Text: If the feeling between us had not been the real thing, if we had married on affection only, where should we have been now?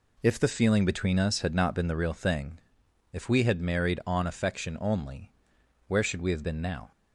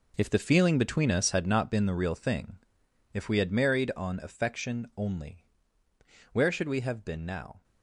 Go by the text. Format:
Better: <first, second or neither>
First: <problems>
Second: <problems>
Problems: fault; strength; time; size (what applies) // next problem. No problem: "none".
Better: first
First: none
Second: gets quieter; strong; throughout; 12 dB